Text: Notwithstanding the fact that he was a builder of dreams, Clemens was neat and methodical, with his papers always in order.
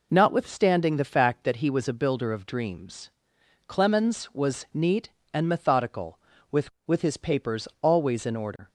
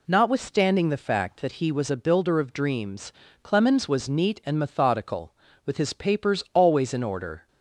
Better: second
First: says "with" twice; at 6.8 s // pauses between "papers" and "always"; slight; at 7.6 s; 0.16 s long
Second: none

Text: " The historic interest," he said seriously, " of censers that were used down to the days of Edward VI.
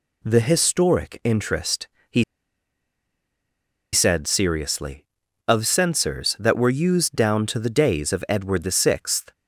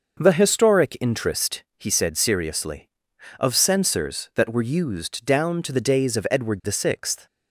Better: second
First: pauses between "he" and "said"; strong; at 2.2 s; 1.7 s long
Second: none

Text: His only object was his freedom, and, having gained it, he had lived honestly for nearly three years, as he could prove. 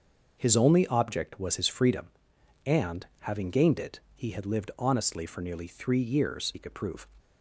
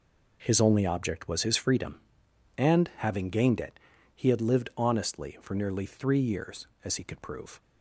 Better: second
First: starts louder than the rest; until 1.4 s; 6.5 dB // skips "as"; at 6.5 s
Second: none

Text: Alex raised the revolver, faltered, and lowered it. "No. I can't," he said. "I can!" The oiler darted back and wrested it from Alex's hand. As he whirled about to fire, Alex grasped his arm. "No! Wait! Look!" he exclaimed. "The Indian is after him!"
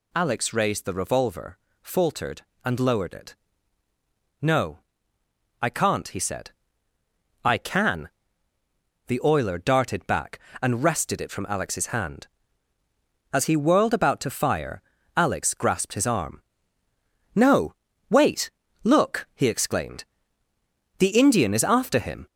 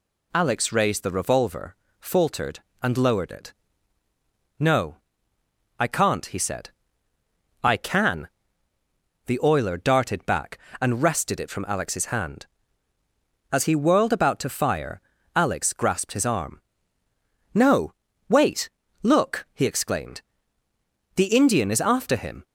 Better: second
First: gets louder; slight; throughout; 3 dB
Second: none

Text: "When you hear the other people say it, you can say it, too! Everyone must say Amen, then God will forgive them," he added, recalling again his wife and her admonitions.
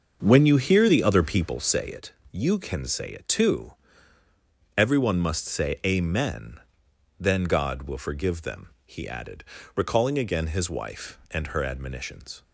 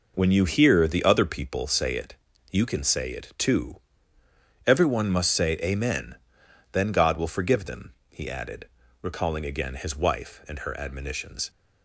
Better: second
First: starts louder than the rest; until 1.7 s; 6.5 dB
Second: none

